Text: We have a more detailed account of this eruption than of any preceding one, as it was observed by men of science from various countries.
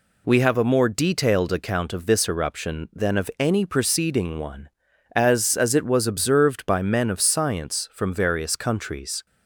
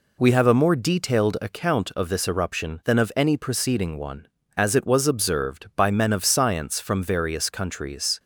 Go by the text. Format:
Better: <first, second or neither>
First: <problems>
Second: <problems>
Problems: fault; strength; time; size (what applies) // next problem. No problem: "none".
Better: second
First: says "as" twice; at 5.5 s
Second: none